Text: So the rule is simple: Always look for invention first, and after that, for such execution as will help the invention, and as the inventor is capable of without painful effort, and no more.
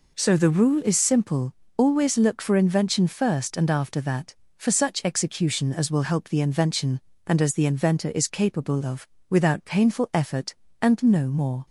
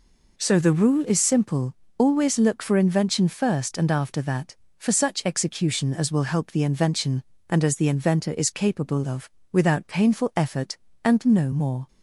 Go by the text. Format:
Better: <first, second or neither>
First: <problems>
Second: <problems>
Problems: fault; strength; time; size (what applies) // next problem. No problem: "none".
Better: neither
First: pauses between "of" and "without"; slight; at 9.0 s; 0.22 s long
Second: pauses between "of" and "without"; slight; at 9.3 s; 0.22 s long